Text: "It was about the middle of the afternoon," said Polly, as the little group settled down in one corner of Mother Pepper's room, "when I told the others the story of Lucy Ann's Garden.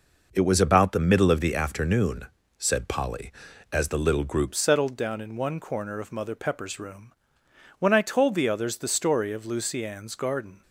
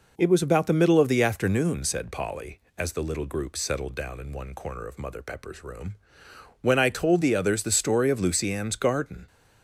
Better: second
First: changes voice at "settled"; from 4.5 s on; 6.1 s long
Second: none

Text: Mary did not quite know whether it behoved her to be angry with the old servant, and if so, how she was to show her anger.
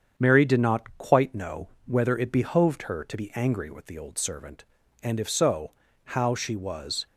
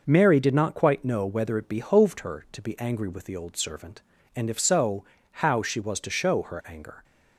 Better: second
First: starts louder than the rest; strong; until 1.1 s; 7.5 dB // pauses between "know" and "whether"; slight; at 1.6 s; 0.18 s long // stops before "to show her anger"; at 7.0 s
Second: none

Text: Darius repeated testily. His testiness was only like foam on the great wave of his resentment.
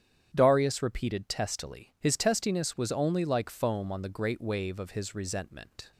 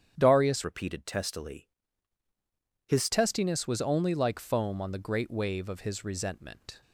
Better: first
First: starts louder than the rest; strong; until 1.3 s; 9.5 dB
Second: starts louder than the rest; strong; until 1.1 s; 9.5 dB // changes voice from "repeated" to "His"; from 0.6 to 3.0 s; 2.4 s long

